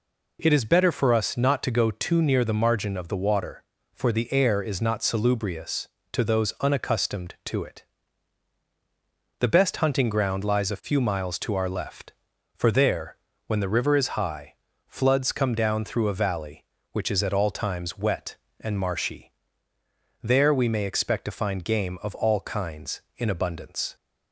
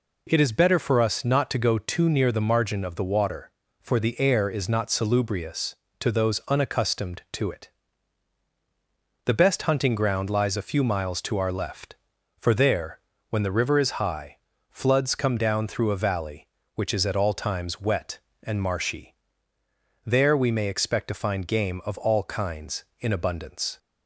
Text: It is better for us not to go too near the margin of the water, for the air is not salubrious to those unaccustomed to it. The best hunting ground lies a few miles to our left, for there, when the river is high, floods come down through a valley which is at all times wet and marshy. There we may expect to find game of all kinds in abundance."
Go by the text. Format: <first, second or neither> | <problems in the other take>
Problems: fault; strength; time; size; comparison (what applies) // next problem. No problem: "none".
neither | none